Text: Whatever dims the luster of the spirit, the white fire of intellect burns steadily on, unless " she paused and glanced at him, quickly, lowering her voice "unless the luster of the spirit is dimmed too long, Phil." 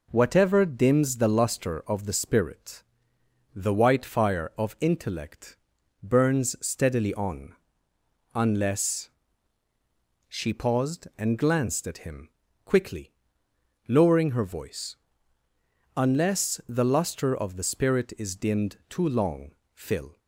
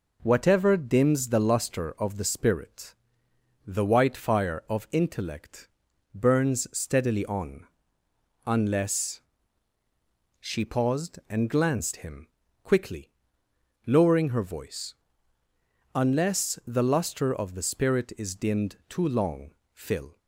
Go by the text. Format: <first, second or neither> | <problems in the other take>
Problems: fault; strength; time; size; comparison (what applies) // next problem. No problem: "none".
first | pauses between "intellect" and "burns"; noticeable; at 5.6 s; 0.46 s long; noticeable in the first // skips "at"; at 11.9 s // pauses between "voice" and "unless"; at 14.9 s; 1.0 s long; also in the first